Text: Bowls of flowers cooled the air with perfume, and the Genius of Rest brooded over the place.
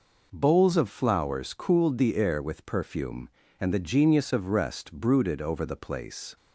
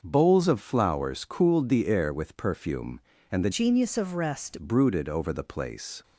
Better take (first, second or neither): first